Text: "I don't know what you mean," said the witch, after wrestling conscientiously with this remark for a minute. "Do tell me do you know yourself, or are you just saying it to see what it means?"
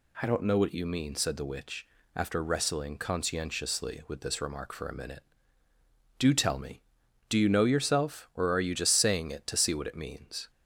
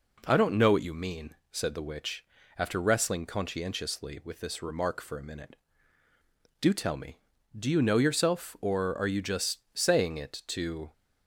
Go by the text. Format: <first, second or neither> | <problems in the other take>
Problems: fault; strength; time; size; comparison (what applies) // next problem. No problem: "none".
first | pauses between "just" and "saying"; slight; at 9.5 s; 0.16 s long // stops before "see what it means"; at 10.9 s